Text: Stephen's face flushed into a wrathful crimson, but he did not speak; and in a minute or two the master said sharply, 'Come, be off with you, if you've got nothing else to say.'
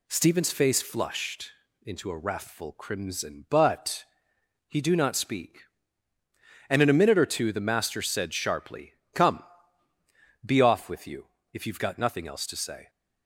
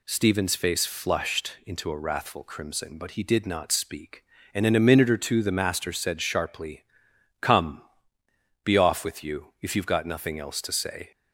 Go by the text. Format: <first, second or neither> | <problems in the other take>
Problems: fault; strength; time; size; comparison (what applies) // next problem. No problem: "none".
second | pauses between "flushed" and "into"; slight; at 1.5 s; 0.32 s long // pauses between "but" and "he"; noticeable; at 4.0 s; 0.64 s long // says "do" for "did"; at 4.8 s